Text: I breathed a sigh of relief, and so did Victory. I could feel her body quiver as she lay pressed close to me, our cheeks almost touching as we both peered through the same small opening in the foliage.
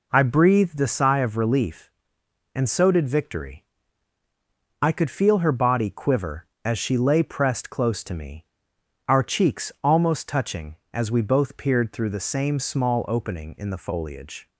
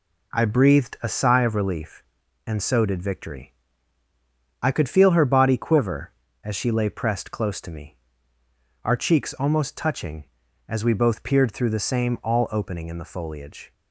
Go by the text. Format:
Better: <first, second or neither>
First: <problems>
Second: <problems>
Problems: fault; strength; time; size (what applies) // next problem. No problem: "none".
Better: first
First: none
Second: says "all" for "small"; at 12.2 s